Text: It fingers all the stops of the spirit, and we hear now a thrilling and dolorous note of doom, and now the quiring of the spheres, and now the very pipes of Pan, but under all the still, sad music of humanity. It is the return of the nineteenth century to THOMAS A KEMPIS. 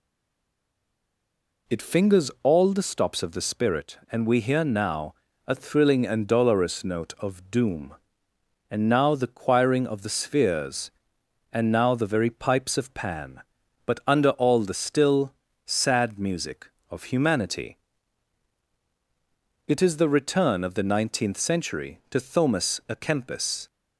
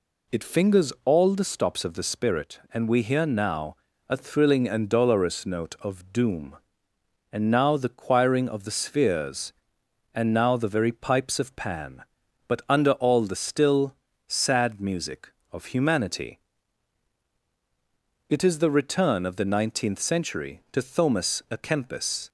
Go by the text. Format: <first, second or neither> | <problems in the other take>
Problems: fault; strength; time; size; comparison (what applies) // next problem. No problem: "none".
second | stays silent before the first word; noticeable; until 1.6 s; 1.6 s long // pauses between "now" and "a"; slight; at 5.1 s; 0.34 s long; slight in the second